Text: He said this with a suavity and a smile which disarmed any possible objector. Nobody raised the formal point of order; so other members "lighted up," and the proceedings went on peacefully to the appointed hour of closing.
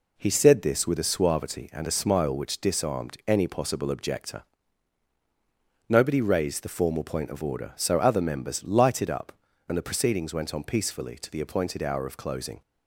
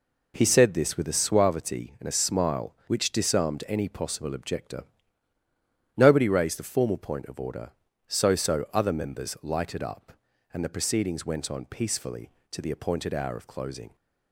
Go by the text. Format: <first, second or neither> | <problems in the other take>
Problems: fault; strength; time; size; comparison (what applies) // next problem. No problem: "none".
first | says "so" twice; at 8.3 s